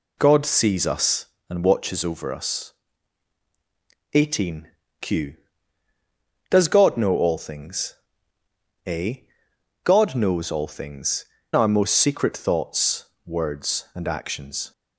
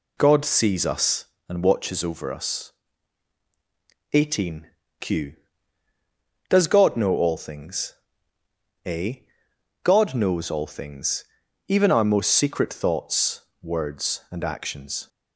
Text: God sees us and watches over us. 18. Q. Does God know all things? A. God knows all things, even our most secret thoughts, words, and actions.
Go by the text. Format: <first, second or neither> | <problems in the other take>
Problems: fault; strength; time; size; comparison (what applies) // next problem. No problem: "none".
second | skips "even"; at 11.3 s